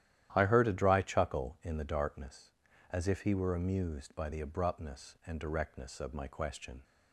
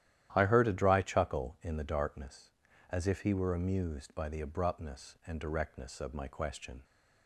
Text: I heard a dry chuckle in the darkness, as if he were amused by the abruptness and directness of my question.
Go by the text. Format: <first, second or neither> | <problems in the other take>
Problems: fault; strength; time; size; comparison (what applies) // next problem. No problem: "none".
neither | starts louder than the rest; strong; the same in both